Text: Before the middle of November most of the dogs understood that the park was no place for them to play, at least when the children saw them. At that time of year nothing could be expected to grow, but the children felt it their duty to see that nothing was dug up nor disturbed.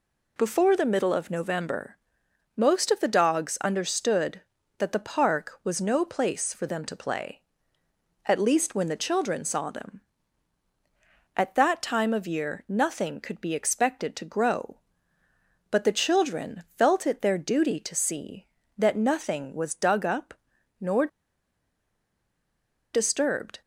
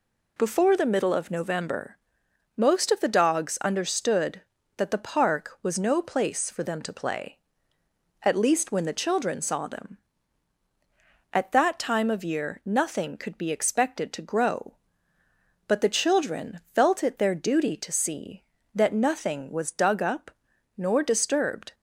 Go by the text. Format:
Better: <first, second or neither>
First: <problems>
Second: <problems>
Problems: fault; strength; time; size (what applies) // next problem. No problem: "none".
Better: second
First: pauses between "November" and "most"; noticeable; at 1.9 s; 0.58 s long // pauses between "up" and "nor"; at 20.3 s; 0.44 s long // pauses between "nor" and "disturbed"; strong; at 21.0 s; 1.8 s long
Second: pauses between "November" and "most"; noticeable; at 1.9 s; 0.58 s long // pauses between "up" and "nor"; at 20.3 s; 0.44 s long